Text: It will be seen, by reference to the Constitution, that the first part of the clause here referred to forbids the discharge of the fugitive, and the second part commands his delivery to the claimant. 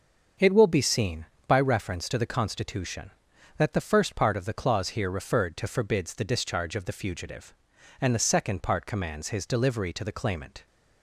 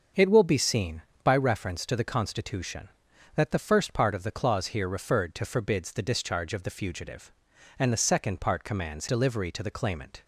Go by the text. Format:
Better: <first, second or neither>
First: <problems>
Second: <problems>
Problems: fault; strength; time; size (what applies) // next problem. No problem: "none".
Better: first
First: starts louder than the rest; until 1.6 s; 6.5 dB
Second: starts louder than the rest; until 1.3 s; 6.5 dB // skips "his"; at 9.0 s